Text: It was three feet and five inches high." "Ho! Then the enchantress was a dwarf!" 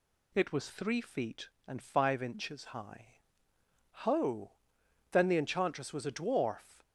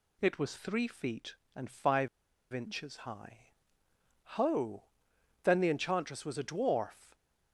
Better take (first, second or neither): first